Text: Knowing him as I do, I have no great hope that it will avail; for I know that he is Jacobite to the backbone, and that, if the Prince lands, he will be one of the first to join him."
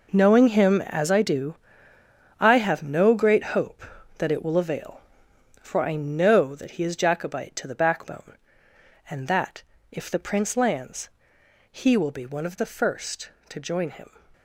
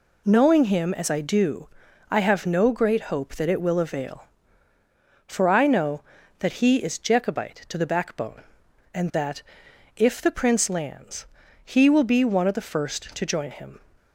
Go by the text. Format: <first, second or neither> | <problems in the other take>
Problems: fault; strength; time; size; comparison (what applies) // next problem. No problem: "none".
second | gets quieter; strong; throughout; 12 dB